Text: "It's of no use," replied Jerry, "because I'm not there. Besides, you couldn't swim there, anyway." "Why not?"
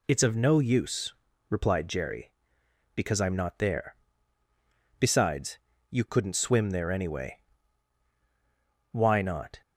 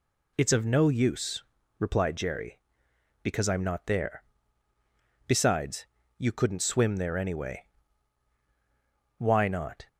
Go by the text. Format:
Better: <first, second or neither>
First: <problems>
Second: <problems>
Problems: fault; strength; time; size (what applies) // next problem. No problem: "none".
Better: neither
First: none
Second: none